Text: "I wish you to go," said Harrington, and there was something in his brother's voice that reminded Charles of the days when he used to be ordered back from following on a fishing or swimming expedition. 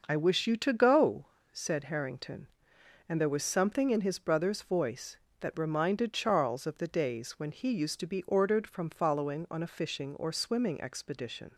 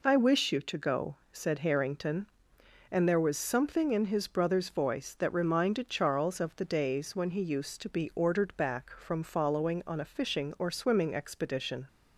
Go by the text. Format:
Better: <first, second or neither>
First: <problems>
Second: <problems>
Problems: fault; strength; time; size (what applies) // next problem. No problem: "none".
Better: second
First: skips "back"; at 8.6 s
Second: none